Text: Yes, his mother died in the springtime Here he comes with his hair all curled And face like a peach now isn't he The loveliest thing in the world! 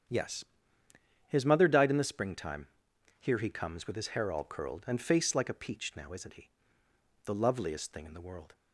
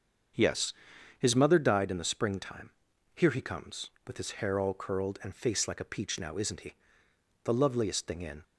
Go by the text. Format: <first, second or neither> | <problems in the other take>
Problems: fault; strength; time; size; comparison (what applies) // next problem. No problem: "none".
first | starts louder than the rest; until 1.8 s; 7 dB; strong in the first // pauses between "springtime" and "Here"; noticeable; at 2.6 s; 0.46 s long; noticeable in the first // pauses between "he" and "The"; noticeable; at 6.7 s; 0.70 s long; noticeable in the first // stops before "the world"; at 8.4 s